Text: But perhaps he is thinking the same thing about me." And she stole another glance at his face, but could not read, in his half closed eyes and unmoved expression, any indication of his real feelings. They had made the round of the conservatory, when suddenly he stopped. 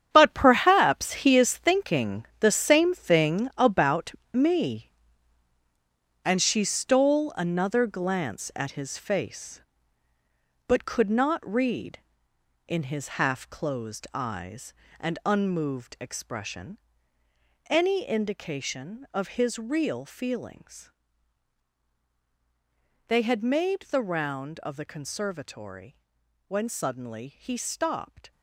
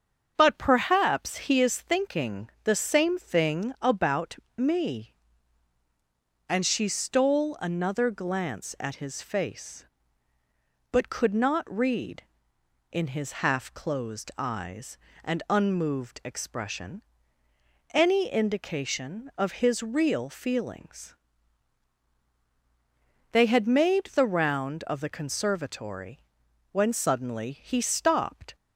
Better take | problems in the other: second | gets quieter; strong; throughout; 12 dB // starts louder than the rest; strong; until 1.1 s; 9 dB; strong in the second // pauses between "thinking" and "the"; slight; at 2.2 s; 0.16 s long; slight in the second // pauses between "about" and "me"; slight; at 4.1 s; 0.22 s long; slight in the second

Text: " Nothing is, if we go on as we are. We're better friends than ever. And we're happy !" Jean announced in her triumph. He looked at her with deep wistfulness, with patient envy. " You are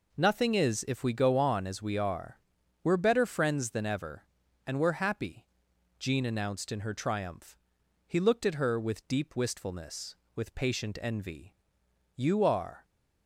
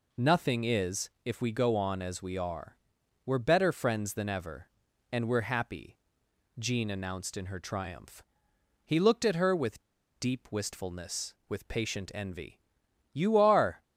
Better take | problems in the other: first | pauses between "with" and "deep"; at 9.8 s; 0.36 s long

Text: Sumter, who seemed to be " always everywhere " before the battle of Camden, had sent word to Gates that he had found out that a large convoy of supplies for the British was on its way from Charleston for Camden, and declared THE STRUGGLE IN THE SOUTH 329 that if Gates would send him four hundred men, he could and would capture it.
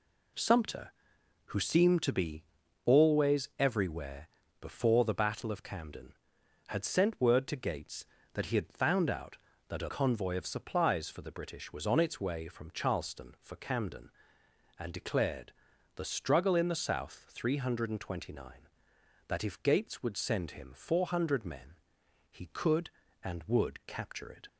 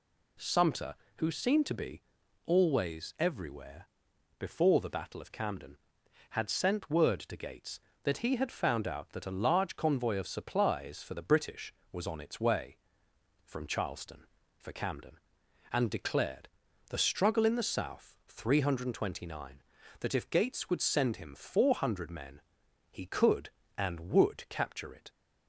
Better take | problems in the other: second | skips "large"; at 9.8 s // pauses between "declared" and "THE"; at 15.5 s; 0.44 s long; also in the second

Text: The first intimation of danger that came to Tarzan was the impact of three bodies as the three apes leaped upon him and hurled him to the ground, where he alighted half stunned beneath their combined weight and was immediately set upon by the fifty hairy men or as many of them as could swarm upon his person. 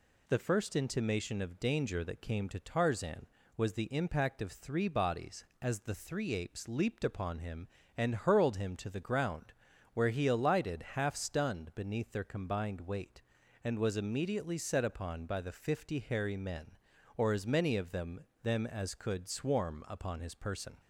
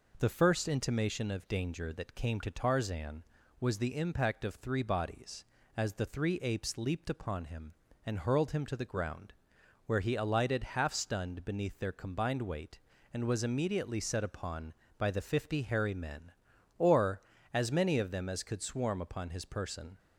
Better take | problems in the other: second | says "them" twice; at 18.4 s

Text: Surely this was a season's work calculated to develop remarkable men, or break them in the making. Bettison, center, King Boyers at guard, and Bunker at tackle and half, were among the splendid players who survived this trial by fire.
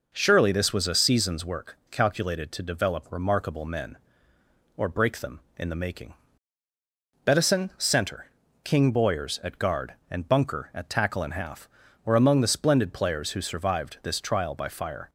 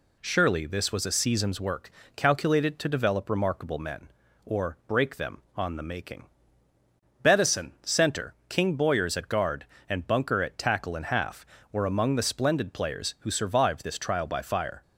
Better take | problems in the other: first | pauses between "work" and "calculated"; slight; at 1.8 s; 0.26 s long // says "on" for "in"; at 5.5 s

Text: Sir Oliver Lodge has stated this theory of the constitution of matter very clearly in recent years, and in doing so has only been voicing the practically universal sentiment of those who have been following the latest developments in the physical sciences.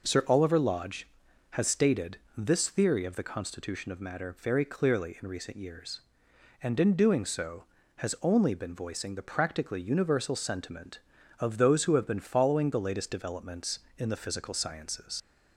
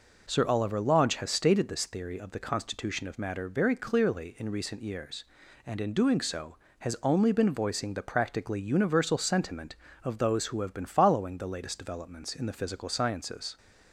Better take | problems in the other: second | pauses between "stated" and "this"; slight; at 2.1 s; 0.18 s long // leaves "sciences" unfinished; at 15.2 s; 90 ms

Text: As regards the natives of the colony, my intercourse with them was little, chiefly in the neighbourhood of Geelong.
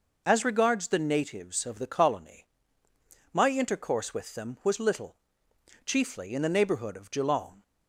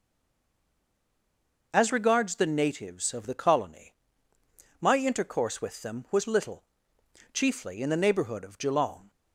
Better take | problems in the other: first | stays silent before the first word; noticeable; until 1.7 s; 1.7 s long

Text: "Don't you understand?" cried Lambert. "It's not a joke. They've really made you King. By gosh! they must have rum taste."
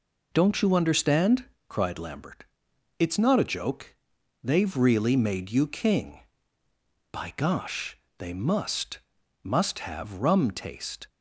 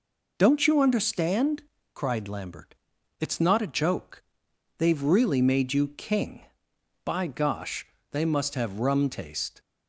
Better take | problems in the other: second | says "must" twice; at 9.4 s

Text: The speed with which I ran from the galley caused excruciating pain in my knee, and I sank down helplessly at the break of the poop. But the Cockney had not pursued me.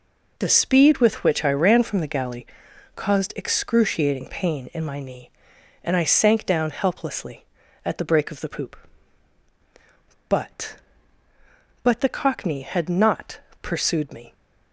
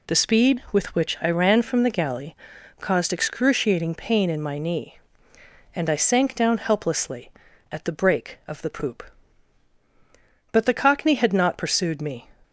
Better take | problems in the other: second | pauses between "galley" and "caused"; noticeable; at 2.4 s; 0.50 s long; noticeable in the second // says "But" twice; at 11.8 s // pauses between "not" and "pursued"; slight; at 13.3 s; 0.22 s long

